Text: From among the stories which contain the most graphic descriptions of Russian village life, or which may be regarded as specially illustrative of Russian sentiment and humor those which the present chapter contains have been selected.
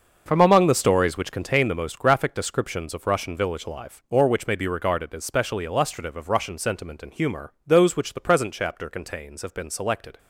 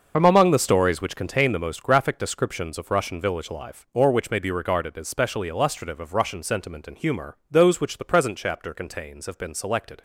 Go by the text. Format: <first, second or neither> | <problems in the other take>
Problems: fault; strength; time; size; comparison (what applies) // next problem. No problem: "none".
first | loses the start of "From"; at 0.1 s; 50 ms // starts louder than the rest; noticeable; until 1.1 s; 6 dB; noticeable in the first